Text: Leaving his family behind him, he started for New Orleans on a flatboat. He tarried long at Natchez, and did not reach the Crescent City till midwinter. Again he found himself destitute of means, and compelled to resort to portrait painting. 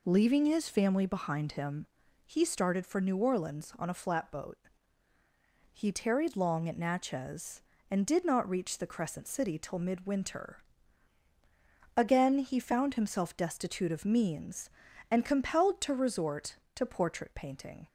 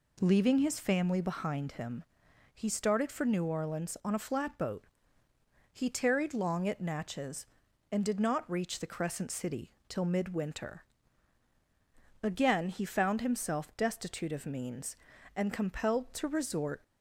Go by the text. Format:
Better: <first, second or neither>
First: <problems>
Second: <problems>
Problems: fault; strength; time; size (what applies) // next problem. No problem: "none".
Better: first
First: none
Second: pauses between "City" and "till"; slight; at 9.7 s; 0.16 s long // stops before "to portrait painting"; at 16.8 s